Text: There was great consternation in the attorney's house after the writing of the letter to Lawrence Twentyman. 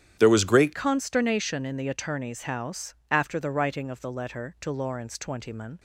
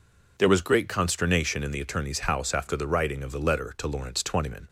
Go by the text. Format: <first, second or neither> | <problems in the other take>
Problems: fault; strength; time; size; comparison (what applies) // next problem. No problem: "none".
second | starts louder than the rest; strong; until 1.2 s; 10 dB // changes voice at "consternation"; from 0.7 s on; 5.0 s long